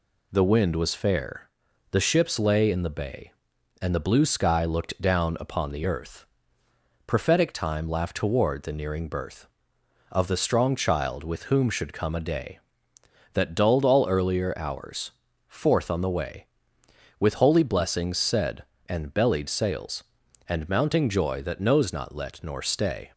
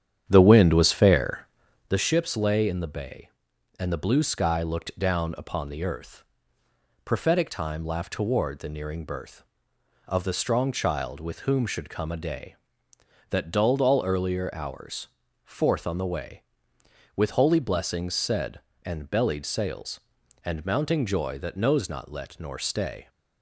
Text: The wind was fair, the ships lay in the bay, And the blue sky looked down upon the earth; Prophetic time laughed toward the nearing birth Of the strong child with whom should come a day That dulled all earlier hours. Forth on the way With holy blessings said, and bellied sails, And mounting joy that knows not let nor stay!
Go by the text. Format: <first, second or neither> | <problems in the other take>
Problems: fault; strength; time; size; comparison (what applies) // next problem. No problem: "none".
first | starts louder than the rest; strong; until 2.0 s; 9.5 dB